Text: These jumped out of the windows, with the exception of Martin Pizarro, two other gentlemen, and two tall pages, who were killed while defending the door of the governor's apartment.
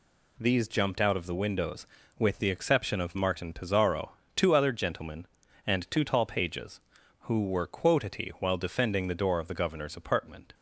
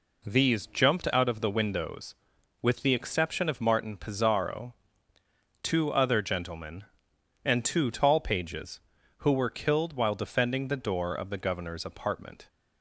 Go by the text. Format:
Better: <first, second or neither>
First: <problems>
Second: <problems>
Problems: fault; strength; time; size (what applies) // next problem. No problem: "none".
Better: second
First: says "quotity" for "killed"; at 7.6 s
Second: none